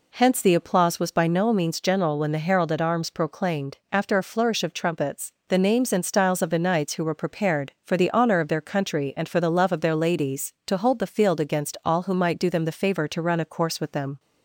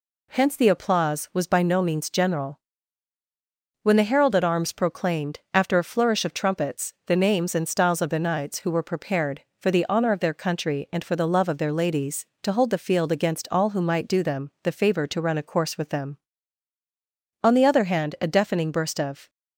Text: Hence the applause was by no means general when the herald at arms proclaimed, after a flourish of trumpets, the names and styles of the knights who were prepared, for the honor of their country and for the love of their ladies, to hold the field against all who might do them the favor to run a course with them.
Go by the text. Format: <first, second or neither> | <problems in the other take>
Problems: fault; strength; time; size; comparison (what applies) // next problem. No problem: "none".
first | pauses between "general" and "when"; at 2.5 s; 1.2 s long // goes on to say "On the other hand a deafening burst of"; strong; from 17.4 s on; 1.8 s long